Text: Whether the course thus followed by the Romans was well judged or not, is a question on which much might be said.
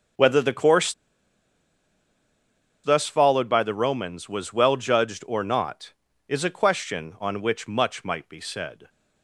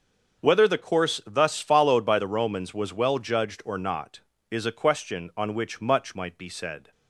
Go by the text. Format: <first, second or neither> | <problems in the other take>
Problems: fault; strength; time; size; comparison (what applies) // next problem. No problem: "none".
second | starts louder than the rest; until 3.1 s; 6.5 dB; also in the second // pauses between "course" and "thus"; strong; at 0.9 s; 1.9 s long